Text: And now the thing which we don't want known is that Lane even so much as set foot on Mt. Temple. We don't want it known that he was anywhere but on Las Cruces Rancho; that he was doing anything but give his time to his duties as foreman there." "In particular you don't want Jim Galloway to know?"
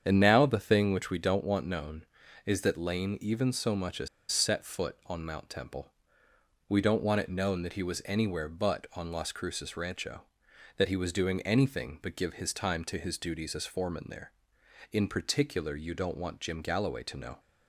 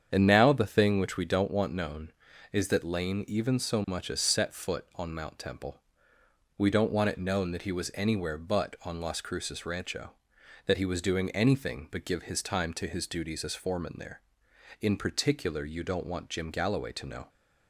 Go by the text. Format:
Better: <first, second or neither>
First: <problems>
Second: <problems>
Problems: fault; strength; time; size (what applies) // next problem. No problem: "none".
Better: second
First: starts louder than the rest; strong; until 1.0 s; 8 dB // pauses between "as" and "set"; slight; at 4.0 s; 0.23 s long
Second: starts louder than the rest; strong; until 1.1 s; 8 dB